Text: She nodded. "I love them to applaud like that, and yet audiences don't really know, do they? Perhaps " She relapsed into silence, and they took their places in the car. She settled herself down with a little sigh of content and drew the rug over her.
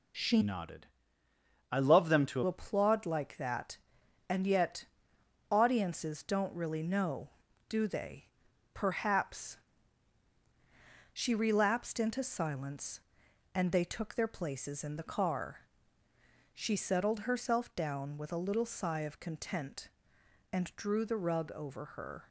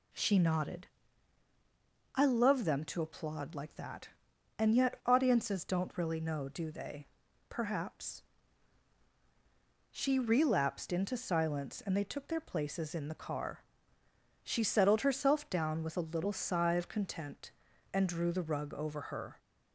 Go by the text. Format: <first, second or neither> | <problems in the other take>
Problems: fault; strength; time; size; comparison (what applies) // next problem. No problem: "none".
second | changes voice from "nodded" to "to"; from 0.4 to 2.4 s; 2.0 s long // pauses between "yet" and "audiences"; noticeable; at 4.8 s; 0.66 s long